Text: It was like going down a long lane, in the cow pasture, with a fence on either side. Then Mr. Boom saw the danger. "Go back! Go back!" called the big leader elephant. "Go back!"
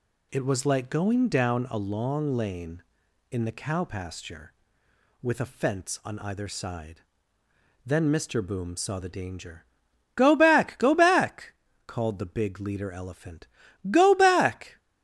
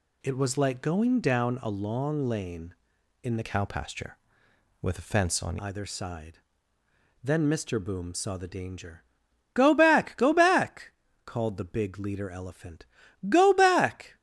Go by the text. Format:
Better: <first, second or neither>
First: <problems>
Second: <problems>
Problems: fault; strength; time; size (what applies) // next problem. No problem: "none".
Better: first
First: none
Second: changes voice from "cow" to "on"; from 3.4 to 5.5 s; 2.1 s long